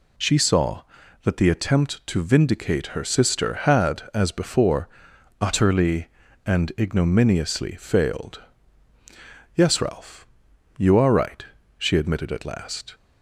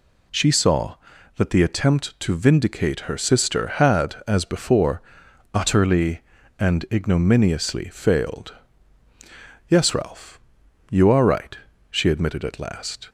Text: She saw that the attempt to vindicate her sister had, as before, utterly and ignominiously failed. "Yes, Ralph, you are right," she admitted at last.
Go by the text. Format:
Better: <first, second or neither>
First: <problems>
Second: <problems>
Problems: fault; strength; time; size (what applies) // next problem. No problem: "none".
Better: neither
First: none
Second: none